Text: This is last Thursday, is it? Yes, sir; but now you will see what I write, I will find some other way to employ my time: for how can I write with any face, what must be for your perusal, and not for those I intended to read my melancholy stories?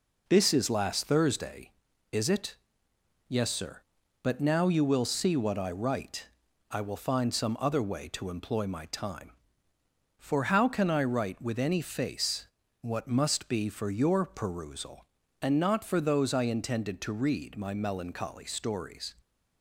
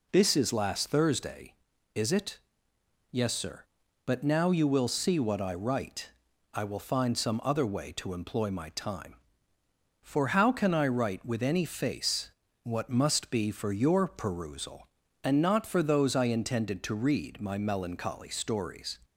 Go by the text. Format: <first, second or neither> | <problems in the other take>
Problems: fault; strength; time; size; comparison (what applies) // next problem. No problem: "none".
second | gets quieter; noticeable; throughout; 5 dB